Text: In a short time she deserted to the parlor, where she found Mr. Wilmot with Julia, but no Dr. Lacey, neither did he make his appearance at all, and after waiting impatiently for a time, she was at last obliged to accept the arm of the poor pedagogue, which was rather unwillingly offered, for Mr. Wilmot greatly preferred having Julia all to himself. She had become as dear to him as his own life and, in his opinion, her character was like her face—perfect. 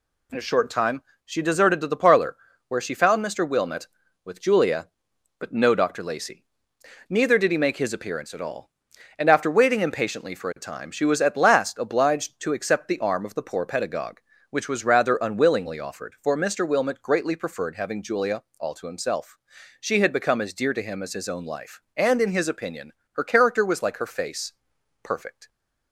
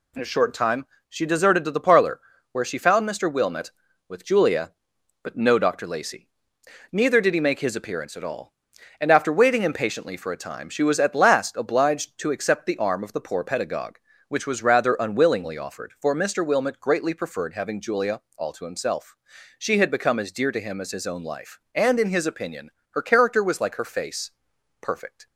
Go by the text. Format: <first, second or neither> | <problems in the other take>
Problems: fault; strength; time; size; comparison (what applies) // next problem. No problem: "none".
neither | pauses between "time" and "she"; slight; the same in both // pauses between "Julia" and "all"; slight; the same in both